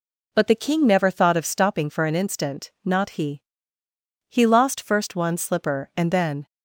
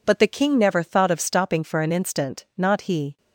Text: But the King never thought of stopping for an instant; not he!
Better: second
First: goes on to say "He lost first one slipper and then"; strong; from 4.2 s on; 2.1 s long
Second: none

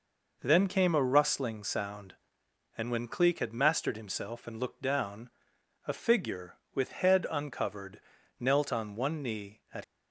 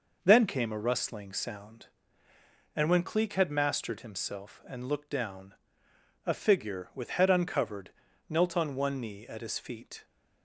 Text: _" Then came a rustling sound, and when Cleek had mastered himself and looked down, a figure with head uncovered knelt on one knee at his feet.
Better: second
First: pauses between "uncovered" and "knelt"; at 7.9 s; 0.40 s long // stops before "his feet"; at 9.8 s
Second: pauses between "uncovered" and "knelt"; at 7.9 s; 0.38 s long

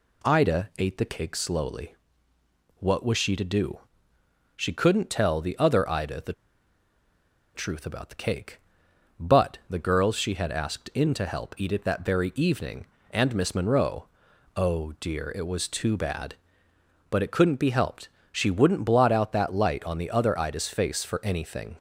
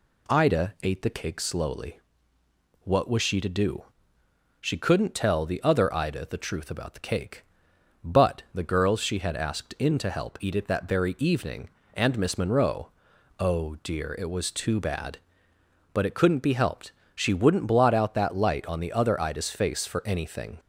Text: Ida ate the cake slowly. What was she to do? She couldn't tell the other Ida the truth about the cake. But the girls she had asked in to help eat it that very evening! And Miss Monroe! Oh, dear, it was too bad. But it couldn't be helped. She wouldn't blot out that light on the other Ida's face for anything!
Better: second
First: pauses between "the" and "truth"; at 6.3 s; 1.2 s long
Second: none

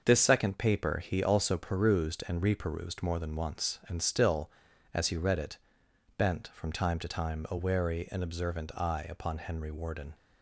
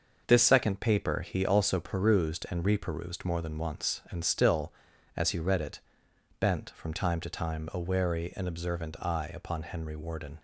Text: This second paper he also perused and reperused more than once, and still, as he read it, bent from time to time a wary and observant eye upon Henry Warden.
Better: neither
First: starts louder than the rest; noticeable; until 1.0 s; 6 dB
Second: starts louder than the rest; noticeable; until 1.2 s; 6 dB

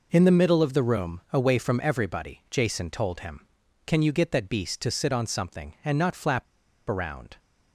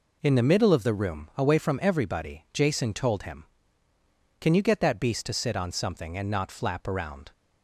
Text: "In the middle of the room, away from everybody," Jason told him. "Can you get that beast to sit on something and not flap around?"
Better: second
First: pauses between "flap" and "around"; at 6.4 s; 0.44 s long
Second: none

